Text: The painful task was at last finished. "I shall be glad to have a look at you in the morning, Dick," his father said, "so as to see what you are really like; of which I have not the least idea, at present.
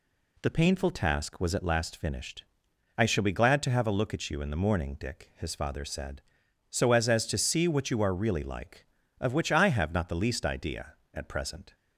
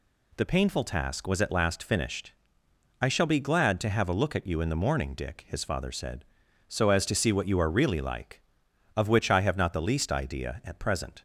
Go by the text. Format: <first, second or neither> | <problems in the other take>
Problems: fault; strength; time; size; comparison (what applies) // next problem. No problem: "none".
second | says "as" twice; at 7.0 s